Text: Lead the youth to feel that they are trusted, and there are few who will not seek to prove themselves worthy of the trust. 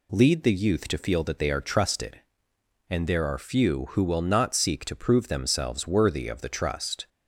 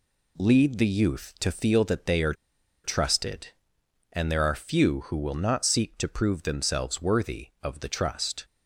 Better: first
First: none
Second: pauses between "are" and "trusted"; noticeable; at 2.3 s; 0.49 s long

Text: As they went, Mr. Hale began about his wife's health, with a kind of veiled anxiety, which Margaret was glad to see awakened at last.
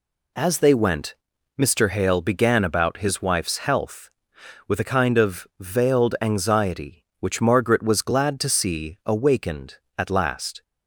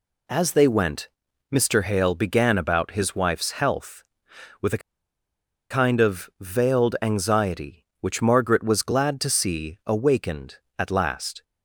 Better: first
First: none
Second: pauses between "a" and "kind"; noticeable; at 4.8 s; 0.91 s long

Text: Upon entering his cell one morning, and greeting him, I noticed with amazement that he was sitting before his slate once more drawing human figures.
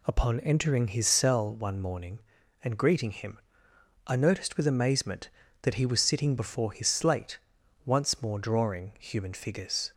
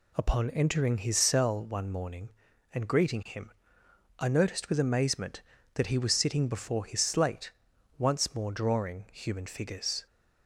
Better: neither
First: pauses between "slate" and "once"; noticeable; at 7.3 s; 0.48 s long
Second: pauses between "slate" and "once"; noticeable; at 7.4 s; 0.48 s long

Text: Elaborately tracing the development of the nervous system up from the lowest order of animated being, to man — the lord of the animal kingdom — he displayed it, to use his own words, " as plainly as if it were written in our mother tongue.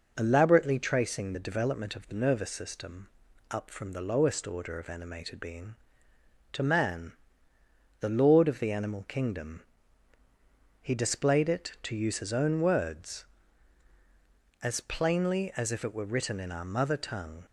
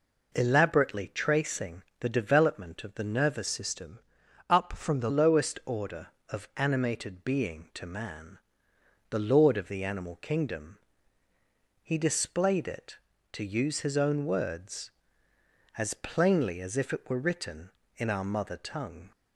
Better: first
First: pauses between "system" and "up"; at 3.0 s; 0.44 s long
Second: pauses between "tracing" and "the"; slight; at 1.8 s; 0.18 s long // changes voice from "system" to "the"; from 3.4 to 5.1 s; 1.7 s long // pauses between "system" and "up"; noticeable; at 3.9 s; 0.50 s long

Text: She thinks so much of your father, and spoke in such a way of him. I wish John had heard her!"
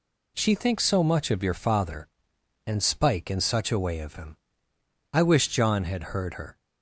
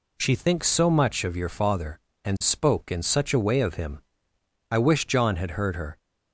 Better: second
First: says "spike" for "spoke"; at 2.8 s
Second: none

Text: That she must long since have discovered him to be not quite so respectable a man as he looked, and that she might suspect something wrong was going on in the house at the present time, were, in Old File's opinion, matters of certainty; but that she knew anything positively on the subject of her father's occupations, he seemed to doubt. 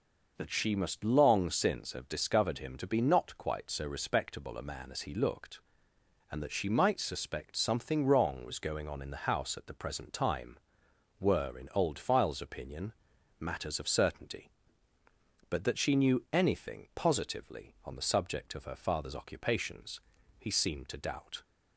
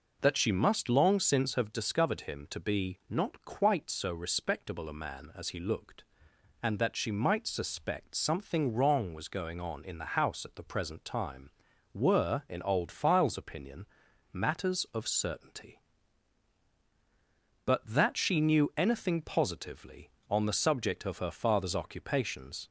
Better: first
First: none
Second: stops before "he seemed to doubt"; at 22.6 s

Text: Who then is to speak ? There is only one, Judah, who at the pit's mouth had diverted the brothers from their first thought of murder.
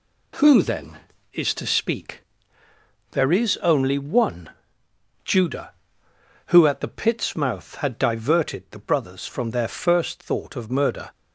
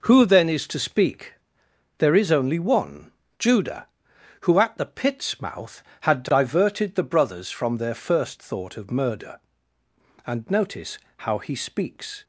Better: first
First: none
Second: goes on to say "And notice how he speaks"; strong; from 10.2 s on; 1.9 s long

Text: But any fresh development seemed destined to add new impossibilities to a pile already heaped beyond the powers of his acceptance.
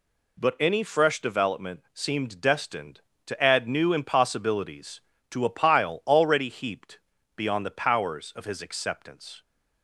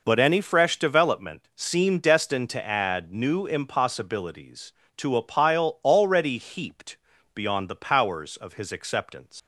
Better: first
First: pauses between "heaped" and "beyond"; slight; at 6.9 s; 0.36 s long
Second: pauses between "heaped" and "beyond"; slight; at 6.9 s; 0.36 s long // leaves "acceptance" unfinished; at 9.3 s; 120 ms

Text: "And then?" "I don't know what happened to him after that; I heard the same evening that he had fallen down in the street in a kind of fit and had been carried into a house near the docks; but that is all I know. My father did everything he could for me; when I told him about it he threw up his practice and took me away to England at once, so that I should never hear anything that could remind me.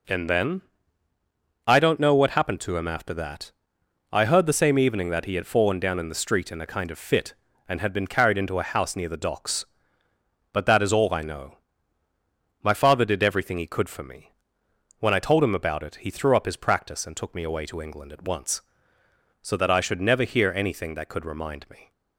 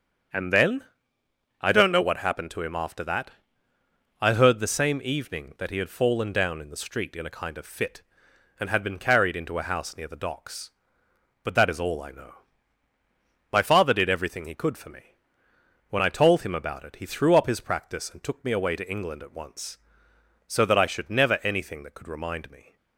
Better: first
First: none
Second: starts louder than the rest; strong; until 2.0 s; 7.5 dB // skips "hear"; at 21.4 s

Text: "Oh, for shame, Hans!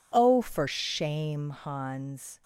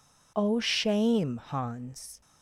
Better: first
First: none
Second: skips "for"; at 0.6 s

